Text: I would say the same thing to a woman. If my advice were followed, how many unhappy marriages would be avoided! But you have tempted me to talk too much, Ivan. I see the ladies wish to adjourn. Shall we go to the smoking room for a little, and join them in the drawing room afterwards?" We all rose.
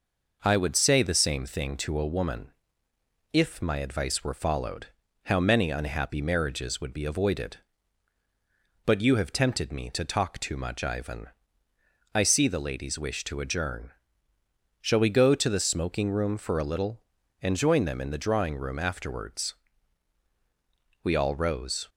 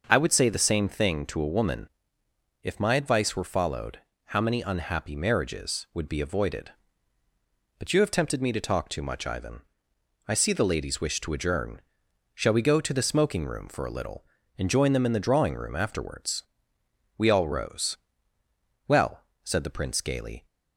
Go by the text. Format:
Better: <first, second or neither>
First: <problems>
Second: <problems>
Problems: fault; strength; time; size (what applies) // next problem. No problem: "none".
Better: first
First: none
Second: starts louder than the rest; until 1.0 s; 6 dB // goes on to say "Well said the Prince gaily"; from 18.8 s on; 1.5 s long